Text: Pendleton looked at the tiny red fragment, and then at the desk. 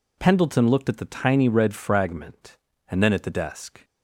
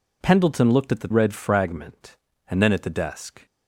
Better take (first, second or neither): first